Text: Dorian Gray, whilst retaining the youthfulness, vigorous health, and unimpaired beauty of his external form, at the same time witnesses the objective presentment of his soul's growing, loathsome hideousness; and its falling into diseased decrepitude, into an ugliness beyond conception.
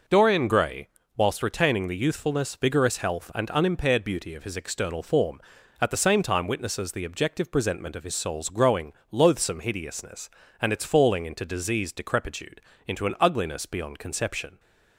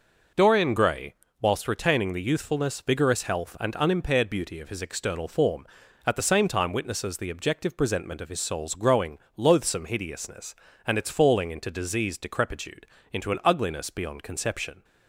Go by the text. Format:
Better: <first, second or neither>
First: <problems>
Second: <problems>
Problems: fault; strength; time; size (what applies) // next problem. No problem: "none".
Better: neither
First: none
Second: none